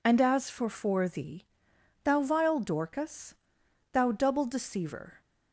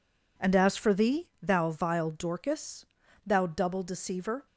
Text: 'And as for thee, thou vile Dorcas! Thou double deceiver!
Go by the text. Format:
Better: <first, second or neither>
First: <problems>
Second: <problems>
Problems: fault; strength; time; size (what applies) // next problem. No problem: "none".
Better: second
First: says "for" twice; at 0.6 s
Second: none